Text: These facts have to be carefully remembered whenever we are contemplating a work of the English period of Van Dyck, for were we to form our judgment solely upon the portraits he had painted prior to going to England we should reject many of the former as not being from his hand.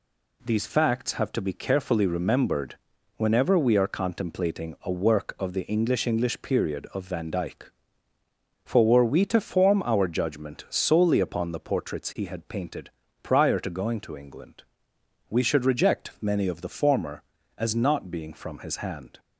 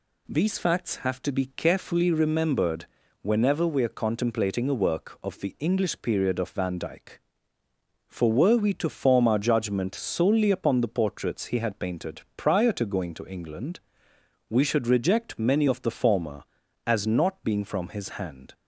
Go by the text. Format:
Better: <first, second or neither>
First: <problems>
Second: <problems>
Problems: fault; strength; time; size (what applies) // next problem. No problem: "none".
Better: second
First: pauses between "remembered" and "whenever"; at 2.7 s; 0.40 s long // says "English" twice; at 6.0 s // pauses between "painted" and "prior"; slight; at 12.8 s; 0.32 s long // pauses between "England" and "we"; noticeable; at 14.6 s; 0.66 s long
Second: pauses between "remembered" and "whenever"; at 2.8 s; 0.38 s long // pauses between "painted" and "prior"; slight; at 12.2 s; 0.16 s long // pauses between "England" and "we"; noticeable; at 13.7 s; 0.70 s long